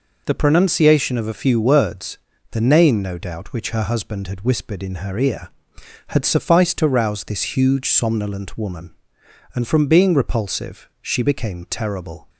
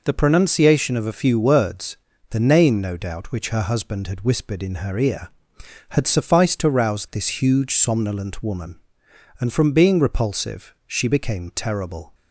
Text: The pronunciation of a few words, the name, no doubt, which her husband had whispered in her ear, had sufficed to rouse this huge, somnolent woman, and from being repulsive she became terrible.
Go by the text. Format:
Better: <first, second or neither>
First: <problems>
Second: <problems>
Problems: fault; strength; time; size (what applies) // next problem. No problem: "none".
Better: neither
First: none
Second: none